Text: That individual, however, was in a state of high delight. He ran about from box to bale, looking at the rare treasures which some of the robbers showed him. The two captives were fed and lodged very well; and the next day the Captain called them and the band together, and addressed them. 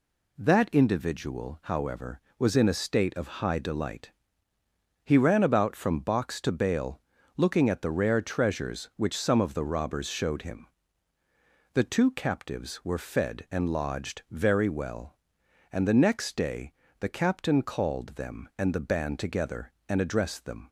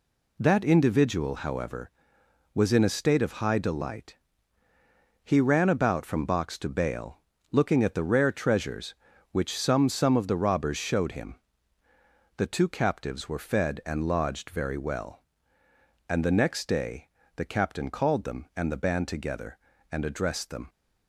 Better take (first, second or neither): first